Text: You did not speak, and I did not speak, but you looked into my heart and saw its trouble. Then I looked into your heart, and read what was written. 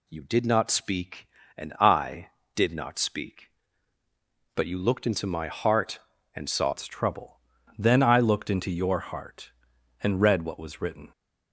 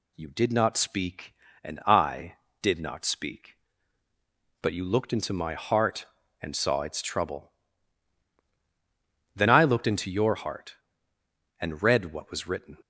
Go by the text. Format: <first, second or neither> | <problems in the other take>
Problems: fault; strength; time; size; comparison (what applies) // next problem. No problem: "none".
second | changes voice at "its"; from 6.7 s on; 4.3 s long